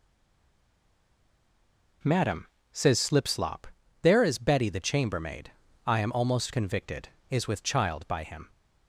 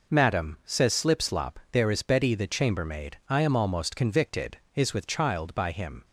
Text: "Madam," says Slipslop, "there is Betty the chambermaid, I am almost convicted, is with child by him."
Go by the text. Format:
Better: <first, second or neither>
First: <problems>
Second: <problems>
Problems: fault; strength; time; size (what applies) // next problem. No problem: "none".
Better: second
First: stays silent before the first word; noticeable; until 2.0 s; 2.0 s long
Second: none